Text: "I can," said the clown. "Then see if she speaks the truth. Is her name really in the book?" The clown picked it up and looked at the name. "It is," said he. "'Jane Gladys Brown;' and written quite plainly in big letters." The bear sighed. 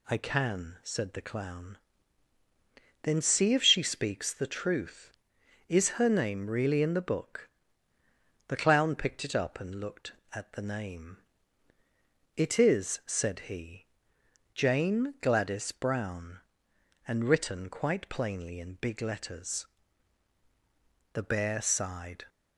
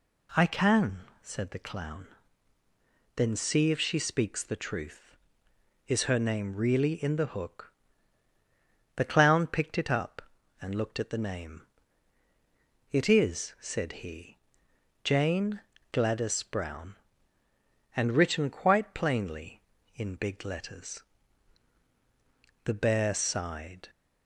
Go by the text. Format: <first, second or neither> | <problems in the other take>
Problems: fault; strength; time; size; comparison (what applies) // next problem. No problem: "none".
first | says "hook" for "book"; at 7.3 s // pauses between "Jane" and "Gladys"; slight; at 15.6 s; 0.30 s long